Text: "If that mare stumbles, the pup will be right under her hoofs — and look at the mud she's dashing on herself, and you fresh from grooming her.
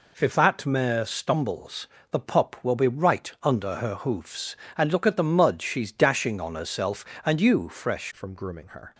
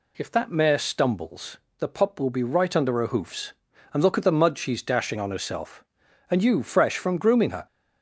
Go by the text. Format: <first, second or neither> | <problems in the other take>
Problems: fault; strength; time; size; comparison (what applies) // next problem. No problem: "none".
second | changes voice at "from"; from 8.1 s on; 0.8 s long